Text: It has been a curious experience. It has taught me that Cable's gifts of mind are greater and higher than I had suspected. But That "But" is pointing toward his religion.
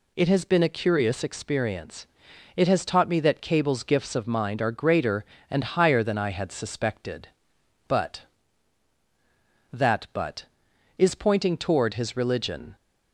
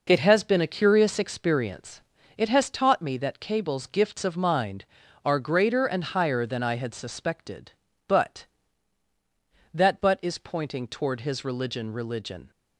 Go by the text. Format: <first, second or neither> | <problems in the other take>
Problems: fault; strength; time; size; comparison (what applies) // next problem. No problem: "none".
first | says "religion" twice; at 11.9 s